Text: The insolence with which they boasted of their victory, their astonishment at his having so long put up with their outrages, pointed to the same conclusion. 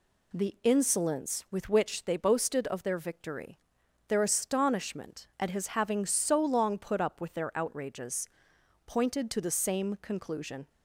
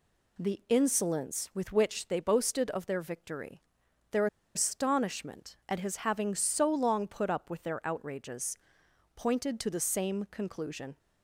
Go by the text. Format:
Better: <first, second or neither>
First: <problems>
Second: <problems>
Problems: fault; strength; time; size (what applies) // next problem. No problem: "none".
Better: first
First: none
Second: pauses between "their" and "astonishment"; slight; at 4.2 s; 0.29 s long